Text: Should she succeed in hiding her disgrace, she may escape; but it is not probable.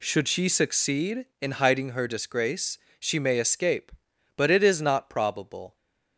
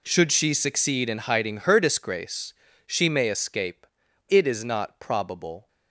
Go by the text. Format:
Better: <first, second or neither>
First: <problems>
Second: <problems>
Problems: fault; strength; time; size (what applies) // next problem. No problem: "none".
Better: first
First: none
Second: skips "but"; at 4.0 s